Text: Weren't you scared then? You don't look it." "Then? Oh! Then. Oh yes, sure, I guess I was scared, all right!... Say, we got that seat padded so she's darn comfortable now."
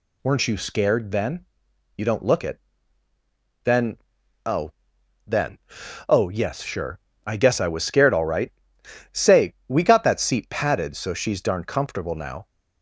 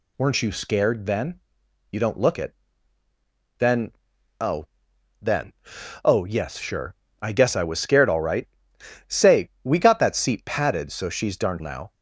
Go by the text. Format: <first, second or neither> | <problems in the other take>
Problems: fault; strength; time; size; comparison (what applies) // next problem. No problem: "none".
first | skips "comfortable"; at 11.5 s